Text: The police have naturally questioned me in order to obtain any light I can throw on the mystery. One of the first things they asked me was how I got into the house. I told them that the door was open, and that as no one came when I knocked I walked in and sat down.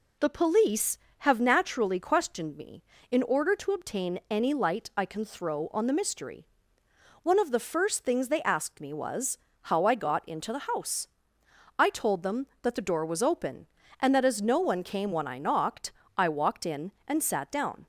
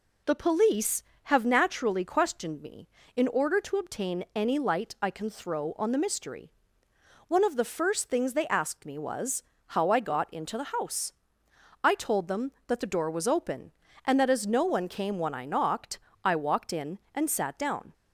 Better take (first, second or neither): neither